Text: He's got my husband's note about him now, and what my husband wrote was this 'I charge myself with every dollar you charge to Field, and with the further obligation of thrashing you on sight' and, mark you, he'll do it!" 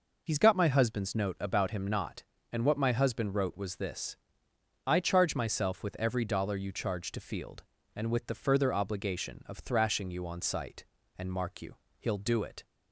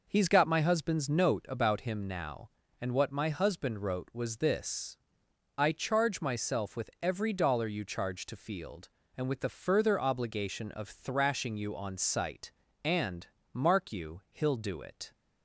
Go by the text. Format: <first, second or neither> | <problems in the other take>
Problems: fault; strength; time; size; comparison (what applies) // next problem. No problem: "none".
second | says "not" for "now"; at 1.8 s // pauses between "this" and "I"; noticeable; at 4.1 s; 0.72 s long; noticeable in the second